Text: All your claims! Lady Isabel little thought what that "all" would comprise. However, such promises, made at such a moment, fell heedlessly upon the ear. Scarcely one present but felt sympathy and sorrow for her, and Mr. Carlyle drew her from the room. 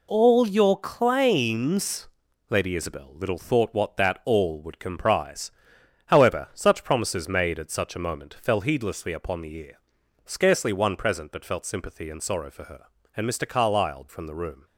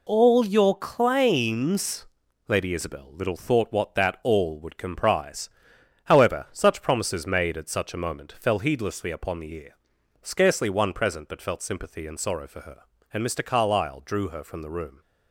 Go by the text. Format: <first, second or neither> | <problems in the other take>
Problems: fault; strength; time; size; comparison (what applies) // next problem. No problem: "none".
second | skips "drew her"; at 14.0 s